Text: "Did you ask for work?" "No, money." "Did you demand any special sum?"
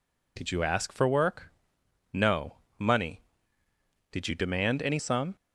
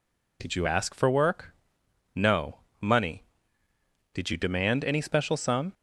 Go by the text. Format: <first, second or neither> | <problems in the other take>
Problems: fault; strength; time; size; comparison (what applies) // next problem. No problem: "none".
second | skips "special"; at 4.9 s